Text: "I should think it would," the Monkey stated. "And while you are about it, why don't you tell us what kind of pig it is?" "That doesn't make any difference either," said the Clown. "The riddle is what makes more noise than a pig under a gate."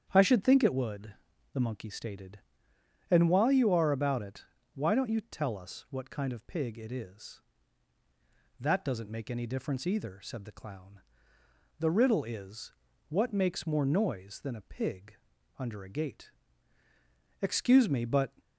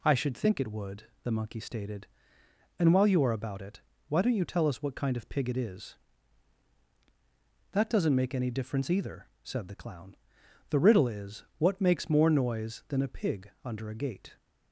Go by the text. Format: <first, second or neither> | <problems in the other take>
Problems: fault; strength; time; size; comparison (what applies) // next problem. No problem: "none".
second | starts louder than the rest; strong; until 1.1 s; 8.5 dB // pauses between "is" and "what"; at 12.7 s; 0.38 s long // pauses between "pig" and "under"; at 15.1 s; 0.42 s long // goes on to say "Excuse me but"; noticeable; from 17.4 s on; 0.90 s long